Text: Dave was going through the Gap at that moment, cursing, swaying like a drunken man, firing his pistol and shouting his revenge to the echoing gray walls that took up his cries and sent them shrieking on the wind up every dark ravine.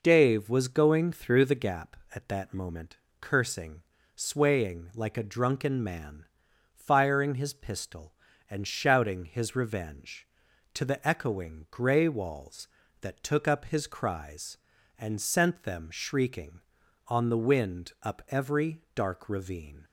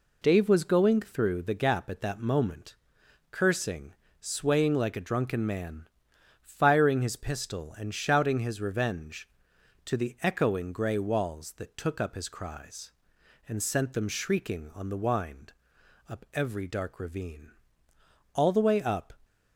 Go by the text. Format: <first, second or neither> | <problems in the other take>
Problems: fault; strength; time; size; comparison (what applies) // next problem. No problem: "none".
first | pauses between "wind" and "up"; noticeable; at 15.5 s; 0.58 s long // goes on to say "All the way up"; noticeable; from 18.3 s on; 0.80 s long